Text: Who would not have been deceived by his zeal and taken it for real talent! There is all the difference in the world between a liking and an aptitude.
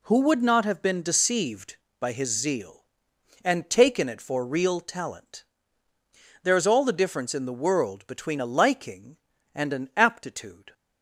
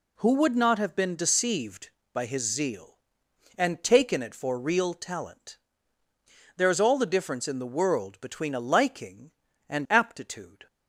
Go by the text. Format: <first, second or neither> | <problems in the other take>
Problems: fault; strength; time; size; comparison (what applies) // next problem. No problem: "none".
first | skips "an"; at 9.8 s